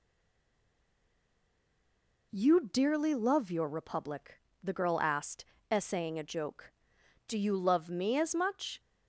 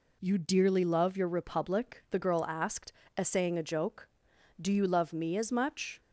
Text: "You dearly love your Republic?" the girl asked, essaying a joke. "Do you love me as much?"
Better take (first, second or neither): second